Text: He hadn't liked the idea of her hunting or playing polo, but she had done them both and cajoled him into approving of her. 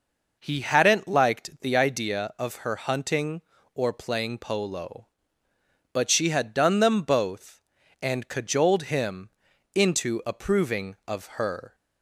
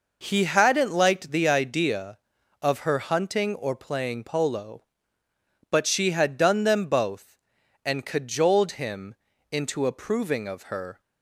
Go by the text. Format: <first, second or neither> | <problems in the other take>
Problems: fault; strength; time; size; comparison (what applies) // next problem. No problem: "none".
neither | pauses between "him" and "into"; the same in both